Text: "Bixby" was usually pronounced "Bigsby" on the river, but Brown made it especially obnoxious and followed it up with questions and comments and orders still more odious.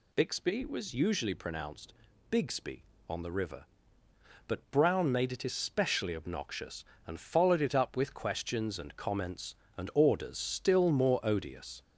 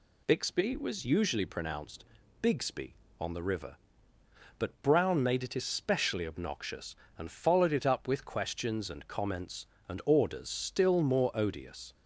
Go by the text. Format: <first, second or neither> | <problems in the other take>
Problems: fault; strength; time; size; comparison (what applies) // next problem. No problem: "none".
second | gets louder; noticeable; throughout; 5 dB // pauses between "pronounced" and "Bigsby"; slight; at 1.9 s; 0.36 s long; slight in the second